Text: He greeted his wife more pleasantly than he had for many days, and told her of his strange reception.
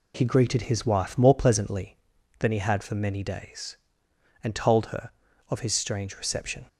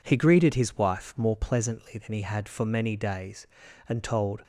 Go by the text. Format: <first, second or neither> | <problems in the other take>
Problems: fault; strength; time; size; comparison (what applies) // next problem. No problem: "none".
first | stops before "her of his strange reception"; at 4.4 s